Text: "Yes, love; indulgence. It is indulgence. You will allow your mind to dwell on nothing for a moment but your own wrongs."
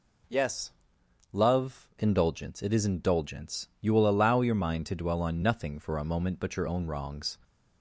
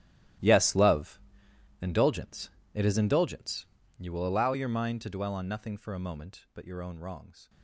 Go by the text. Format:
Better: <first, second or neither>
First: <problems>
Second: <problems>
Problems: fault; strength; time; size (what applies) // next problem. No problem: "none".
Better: first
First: none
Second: gets quieter; strong; throughout; 16 dB